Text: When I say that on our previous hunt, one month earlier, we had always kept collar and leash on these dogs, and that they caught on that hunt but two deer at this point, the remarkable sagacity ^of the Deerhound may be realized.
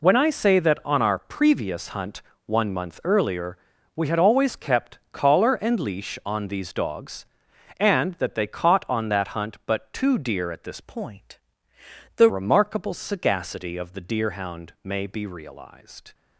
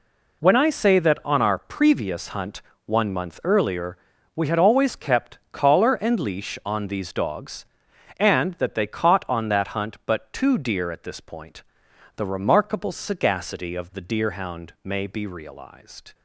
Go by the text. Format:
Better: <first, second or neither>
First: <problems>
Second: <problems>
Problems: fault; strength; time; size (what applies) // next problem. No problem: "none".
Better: second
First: pauses between "kept" and "collar"; slight; at 4.9 s; 0.16 s long // changes voice from "point" to "the"; from 10.8 to 12.2 s; 1.4 s long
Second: pauses between "kept" and "collar"; slight; at 5.3 s; 0.16 s long